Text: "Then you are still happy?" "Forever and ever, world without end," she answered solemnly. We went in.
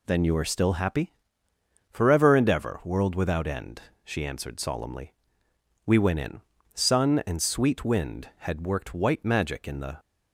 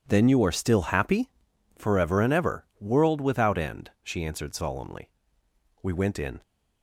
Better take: second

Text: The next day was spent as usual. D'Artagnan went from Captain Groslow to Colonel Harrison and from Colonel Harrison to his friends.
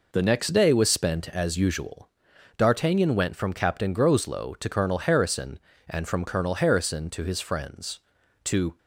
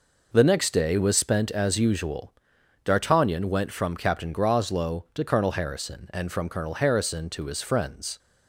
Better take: second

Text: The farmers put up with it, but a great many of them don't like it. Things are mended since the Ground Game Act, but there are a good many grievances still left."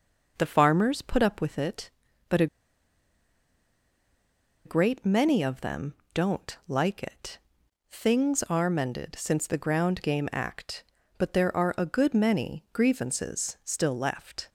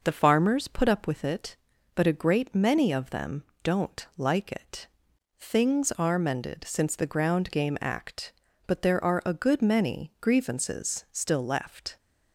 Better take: second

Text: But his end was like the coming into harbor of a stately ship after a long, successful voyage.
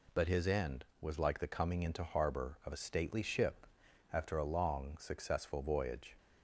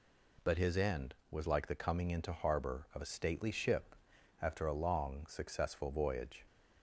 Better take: neither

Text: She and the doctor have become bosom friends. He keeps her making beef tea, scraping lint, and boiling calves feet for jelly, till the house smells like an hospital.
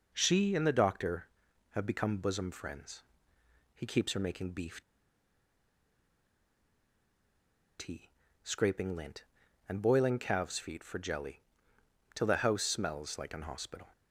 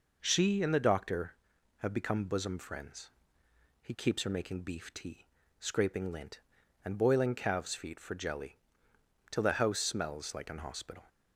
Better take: second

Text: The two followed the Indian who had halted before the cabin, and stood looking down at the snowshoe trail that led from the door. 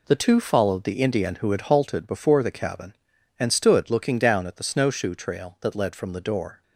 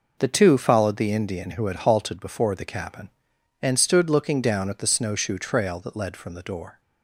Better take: neither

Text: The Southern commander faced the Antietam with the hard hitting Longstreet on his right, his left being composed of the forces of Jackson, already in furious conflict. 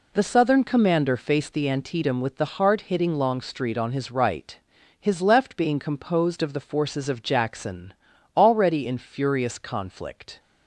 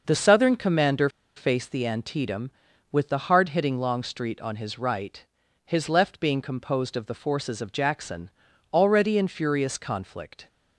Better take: first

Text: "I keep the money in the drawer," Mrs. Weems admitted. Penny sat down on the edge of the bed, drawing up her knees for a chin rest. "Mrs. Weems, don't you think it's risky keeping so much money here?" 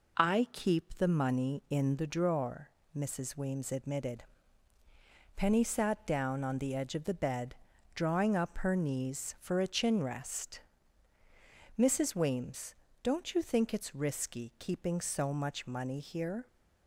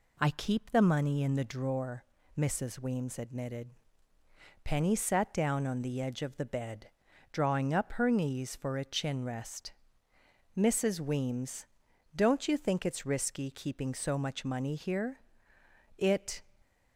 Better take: first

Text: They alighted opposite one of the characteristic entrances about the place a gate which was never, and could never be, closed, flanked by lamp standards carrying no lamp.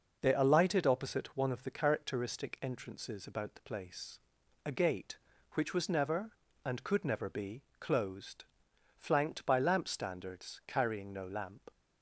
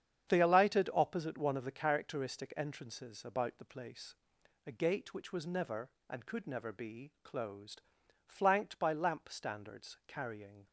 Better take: first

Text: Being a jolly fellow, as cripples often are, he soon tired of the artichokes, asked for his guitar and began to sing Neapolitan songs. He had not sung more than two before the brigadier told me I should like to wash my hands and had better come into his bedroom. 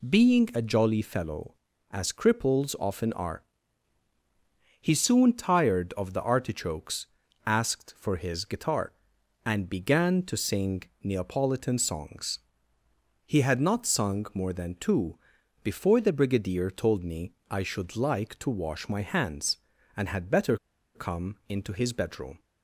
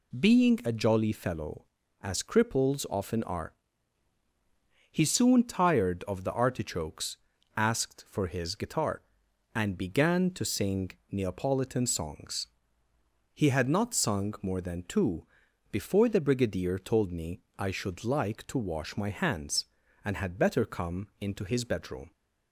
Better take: second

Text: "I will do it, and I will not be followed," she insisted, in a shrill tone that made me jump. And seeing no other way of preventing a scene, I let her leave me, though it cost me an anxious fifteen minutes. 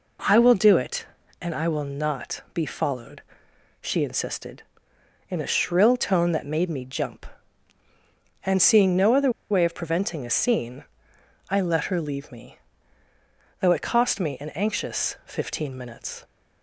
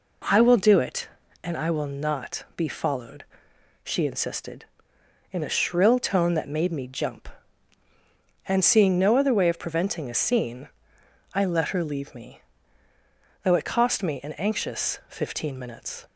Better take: second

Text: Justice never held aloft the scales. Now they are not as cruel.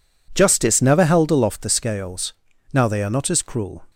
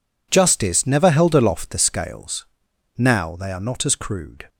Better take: first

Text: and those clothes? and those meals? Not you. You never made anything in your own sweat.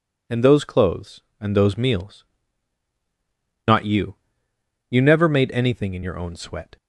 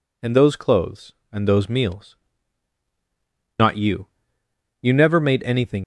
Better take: first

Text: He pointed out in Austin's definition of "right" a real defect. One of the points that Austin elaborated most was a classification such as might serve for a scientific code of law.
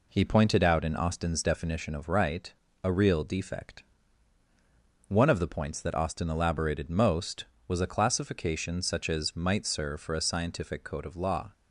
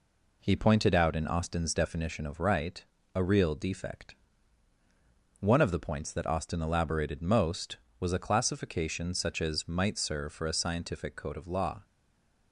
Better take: first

